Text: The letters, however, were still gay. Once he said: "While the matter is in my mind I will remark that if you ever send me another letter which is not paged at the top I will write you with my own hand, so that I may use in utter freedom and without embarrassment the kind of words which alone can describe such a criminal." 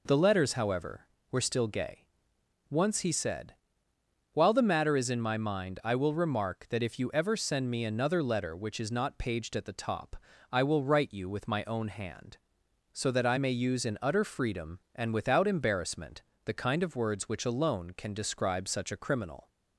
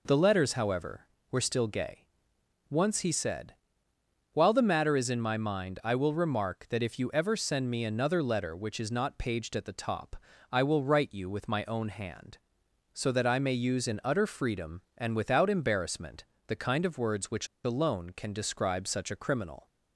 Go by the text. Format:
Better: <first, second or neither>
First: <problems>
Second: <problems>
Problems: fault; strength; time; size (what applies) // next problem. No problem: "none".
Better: first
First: pauses between "top" and "I"; at 10.1 s; 0.38 s long // pauses between "embarrassment" and "the"; slight; at 16.1 s; 0.24 s long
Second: pauses between "top" and "I"; at 10.1 s; 0.38 s long // pauses between "embarrassment" and "the"; slight; at 16.2 s; 0.24 s long // pauses between "which" and "alone"; slight; at 17.4 s; 0.17 s long